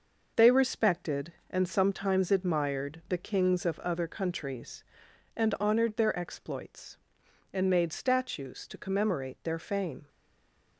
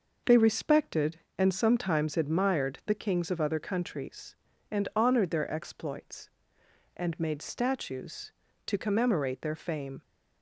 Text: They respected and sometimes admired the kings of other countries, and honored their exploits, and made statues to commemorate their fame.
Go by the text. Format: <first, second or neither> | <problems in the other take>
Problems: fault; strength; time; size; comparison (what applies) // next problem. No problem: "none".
second | stays silent after the last word; slight; from 10.0 s on; 0.7 s long